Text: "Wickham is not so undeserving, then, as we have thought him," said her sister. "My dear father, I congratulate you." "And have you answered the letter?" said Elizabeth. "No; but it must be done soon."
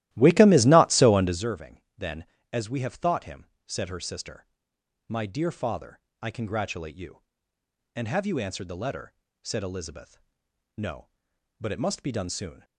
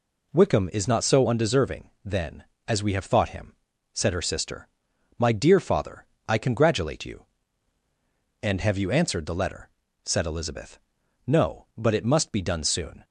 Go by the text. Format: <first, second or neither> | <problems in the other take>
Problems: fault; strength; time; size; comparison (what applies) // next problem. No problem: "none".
second | starts louder than the rest; strong; until 1.5 s; 15 dB